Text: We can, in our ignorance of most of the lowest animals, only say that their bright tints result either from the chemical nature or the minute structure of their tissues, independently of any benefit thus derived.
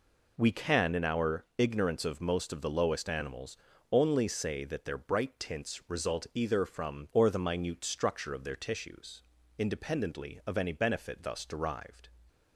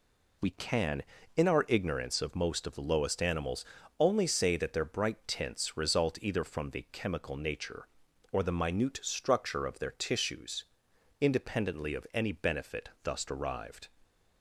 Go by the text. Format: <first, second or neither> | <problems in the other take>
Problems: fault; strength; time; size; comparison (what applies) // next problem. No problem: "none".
second | skips "the chemical nature"; at 7.0 s